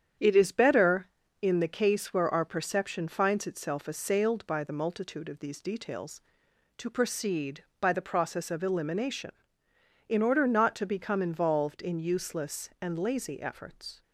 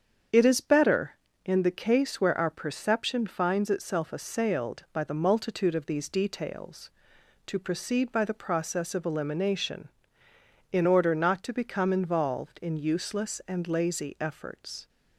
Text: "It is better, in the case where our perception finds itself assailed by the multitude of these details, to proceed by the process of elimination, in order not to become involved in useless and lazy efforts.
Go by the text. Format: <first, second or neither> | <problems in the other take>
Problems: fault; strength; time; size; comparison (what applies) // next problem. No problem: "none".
neither | starts louder than the rest; strong; the same in both